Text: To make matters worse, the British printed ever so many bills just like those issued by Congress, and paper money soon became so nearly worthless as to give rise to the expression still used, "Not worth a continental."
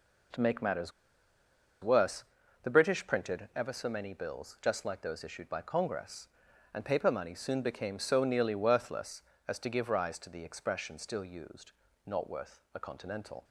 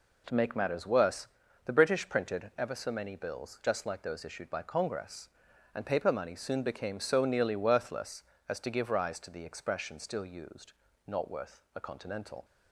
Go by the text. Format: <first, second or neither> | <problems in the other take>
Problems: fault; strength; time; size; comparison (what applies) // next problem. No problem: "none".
second | pauses between "matters" and "worse"; noticeable; at 0.9 s; 0.92 s long